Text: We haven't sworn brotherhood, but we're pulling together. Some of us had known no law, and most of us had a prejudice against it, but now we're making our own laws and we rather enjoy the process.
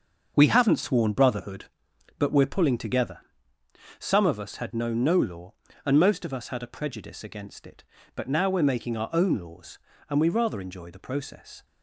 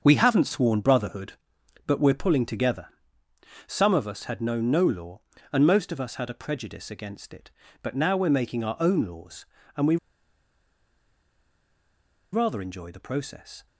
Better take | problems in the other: first | starts louder than the rest; until 1.0 s; 6.5 dB; also in the first // pauses between "we" and "rather"; strong; at 9.9 s; 2.3 s long

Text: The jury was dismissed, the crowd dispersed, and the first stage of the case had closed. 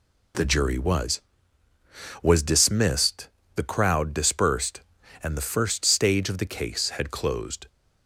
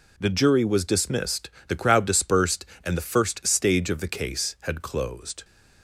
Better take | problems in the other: second | says "was" twice; at 2.2 s

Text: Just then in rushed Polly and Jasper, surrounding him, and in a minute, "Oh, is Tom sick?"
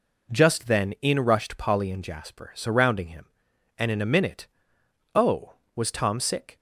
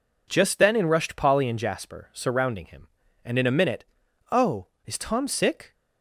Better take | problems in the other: second | says "was" for "is"; at 5.7 s

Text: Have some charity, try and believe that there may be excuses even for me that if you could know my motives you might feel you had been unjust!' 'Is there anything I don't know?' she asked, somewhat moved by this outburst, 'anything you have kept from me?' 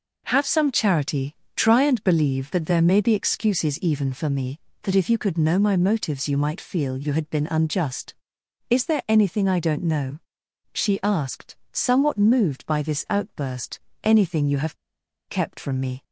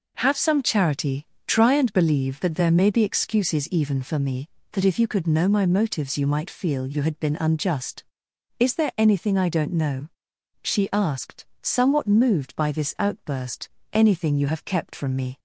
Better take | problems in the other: second | pauses between "have" and "kept"; noticeable; at 14.7 s; 0.54 s long

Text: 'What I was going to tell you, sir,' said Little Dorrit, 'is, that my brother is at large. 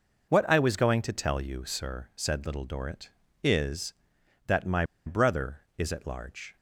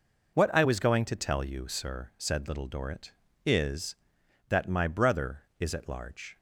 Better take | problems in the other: second | pauses between "my" and "brother"; slight; at 4.8 s; 0.22 s long

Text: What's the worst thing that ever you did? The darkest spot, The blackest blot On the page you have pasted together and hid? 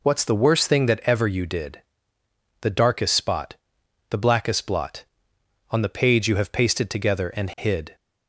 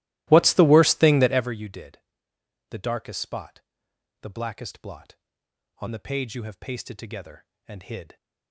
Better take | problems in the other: first | starts louder than the rest; strong; until 1.5 s; 17.5 dB

